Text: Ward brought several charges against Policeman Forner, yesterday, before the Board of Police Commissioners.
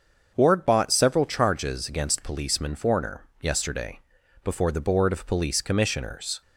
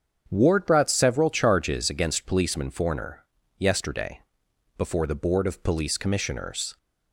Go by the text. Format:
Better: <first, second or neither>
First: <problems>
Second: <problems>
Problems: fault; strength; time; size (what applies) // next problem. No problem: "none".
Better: second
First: starts louder than the rest; until 1.3 s; 6.5 dB // says "bought" for "brought"; at 0.6 s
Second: starts louder than the rest; strong; until 1.2 s; 7 dB